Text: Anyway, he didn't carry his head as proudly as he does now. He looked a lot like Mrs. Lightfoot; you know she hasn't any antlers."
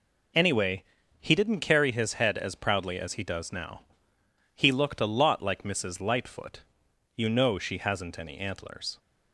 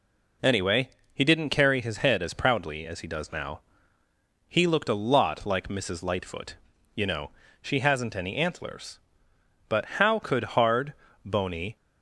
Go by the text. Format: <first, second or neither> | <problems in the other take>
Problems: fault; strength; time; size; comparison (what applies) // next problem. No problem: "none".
first | pauses between "know" and "she"; slight; at 7.2 s; 0.32 s long // goes on to say "But how could hard bony"; strong; from 9.6 s on; 2.0 s long